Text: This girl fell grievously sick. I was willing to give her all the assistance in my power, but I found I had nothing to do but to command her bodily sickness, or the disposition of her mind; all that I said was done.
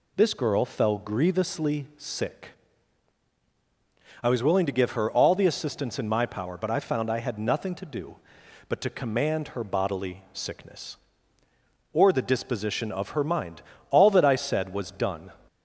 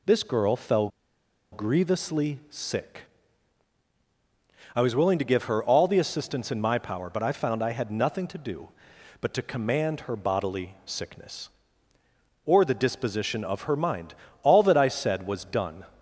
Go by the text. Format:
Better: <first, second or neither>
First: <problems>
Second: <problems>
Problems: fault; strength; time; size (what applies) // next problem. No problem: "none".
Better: first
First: none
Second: pauses between "fell" and "grievously"; noticeable; at 0.8 s; 0.62 s long